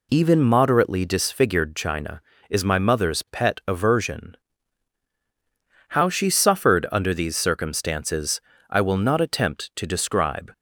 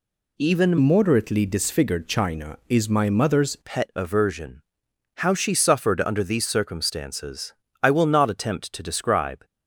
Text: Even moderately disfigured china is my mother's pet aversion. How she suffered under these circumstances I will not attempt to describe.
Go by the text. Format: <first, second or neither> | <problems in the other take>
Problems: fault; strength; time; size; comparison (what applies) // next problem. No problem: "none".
first | changes voice from "moderately" to "mother's"; from 0.7 to 3.5 s; 2.8 s long // pauses between "circumstances" and "I"; slight; at 7.5 s; 0.30 s long; slight in the first